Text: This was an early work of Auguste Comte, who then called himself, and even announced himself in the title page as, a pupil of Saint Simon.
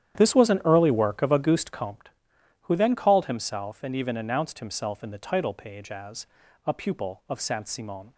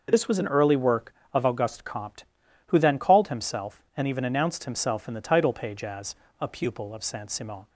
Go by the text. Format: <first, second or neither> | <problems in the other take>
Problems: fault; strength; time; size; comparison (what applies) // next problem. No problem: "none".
second | starts louder than the rest; strong; until 2.1 s; 10.5 dB